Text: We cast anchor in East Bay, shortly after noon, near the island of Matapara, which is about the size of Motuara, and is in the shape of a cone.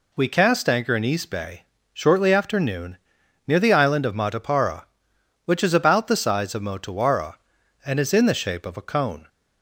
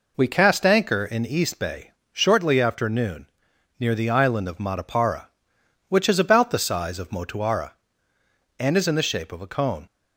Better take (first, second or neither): neither